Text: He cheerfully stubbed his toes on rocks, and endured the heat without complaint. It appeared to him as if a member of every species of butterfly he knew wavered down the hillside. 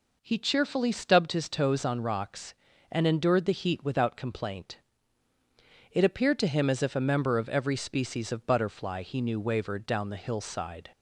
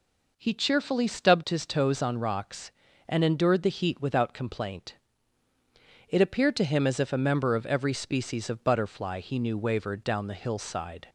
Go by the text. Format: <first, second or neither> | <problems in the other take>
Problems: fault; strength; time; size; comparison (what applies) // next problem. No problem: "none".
neither | none